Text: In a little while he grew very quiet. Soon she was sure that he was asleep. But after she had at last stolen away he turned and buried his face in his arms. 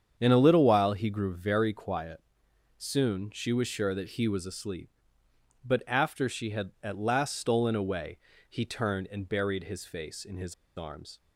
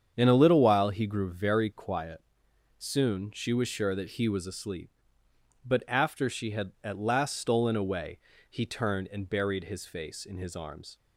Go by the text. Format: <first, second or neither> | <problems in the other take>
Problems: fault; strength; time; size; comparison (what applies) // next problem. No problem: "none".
second | starts louder than the rest; strong; until 1.1 s; 7.5 dB; strong in the second // pauses between "away" and "he"; slight; at 8.1 s; 0.32 s long; slight in the second // pauses between "his" and "arms"; slight; at 10.5 s; 0.22 s long